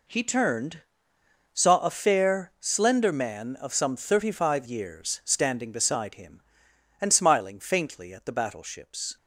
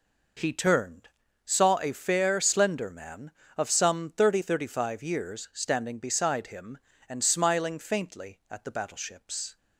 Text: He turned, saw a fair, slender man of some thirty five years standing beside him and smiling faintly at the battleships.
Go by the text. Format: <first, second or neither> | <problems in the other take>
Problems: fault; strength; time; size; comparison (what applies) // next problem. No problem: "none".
first | says "thirty" twice; at 4.4 s